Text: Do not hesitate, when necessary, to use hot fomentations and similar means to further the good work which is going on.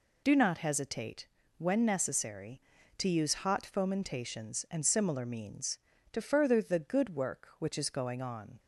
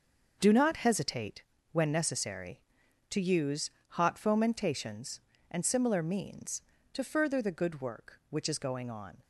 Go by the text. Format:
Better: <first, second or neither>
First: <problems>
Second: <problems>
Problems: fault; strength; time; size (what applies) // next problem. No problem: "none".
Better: first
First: none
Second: gets quieter; strong; throughout; 11 dB // pauses between "use" and "hot"; slight; at 3.7 s; 0.20 s long